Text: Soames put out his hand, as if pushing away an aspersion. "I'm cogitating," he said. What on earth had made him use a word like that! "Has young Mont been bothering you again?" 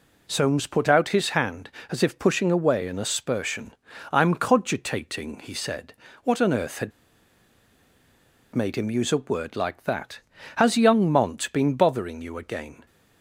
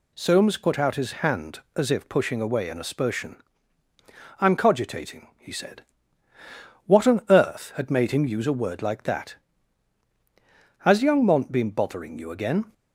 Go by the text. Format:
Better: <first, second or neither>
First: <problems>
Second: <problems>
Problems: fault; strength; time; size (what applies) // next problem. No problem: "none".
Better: second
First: pauses between "had" and "made"; strong; at 6.9 s; 1.6 s long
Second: none